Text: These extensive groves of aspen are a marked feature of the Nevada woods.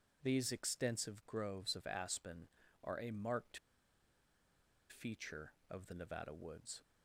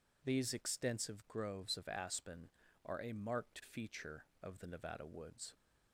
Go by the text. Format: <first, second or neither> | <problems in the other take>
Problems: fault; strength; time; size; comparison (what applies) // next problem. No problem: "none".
second | pauses between "marked" and "feature"; strong; at 3.5 s; 1.3 s long